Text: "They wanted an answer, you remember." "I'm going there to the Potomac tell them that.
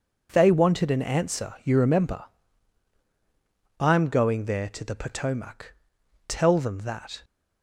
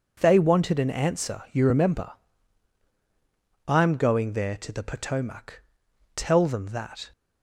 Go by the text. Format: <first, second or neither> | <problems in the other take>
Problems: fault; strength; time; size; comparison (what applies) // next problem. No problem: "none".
neither | pauses between "Potomac" and "tell"; noticeable; the same in both